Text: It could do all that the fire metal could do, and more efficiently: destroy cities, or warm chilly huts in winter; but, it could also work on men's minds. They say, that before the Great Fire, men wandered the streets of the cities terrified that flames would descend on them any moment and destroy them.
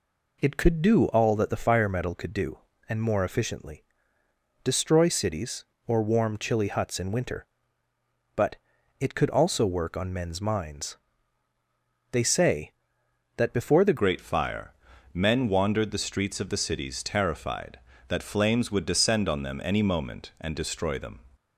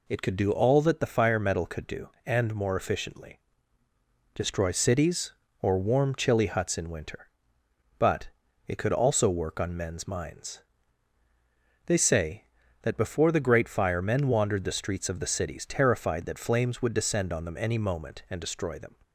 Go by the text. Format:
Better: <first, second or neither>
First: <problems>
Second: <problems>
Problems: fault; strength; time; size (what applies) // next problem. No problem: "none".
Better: second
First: changes voice at "Great"; from 13.9 s on; 7.3 s long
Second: none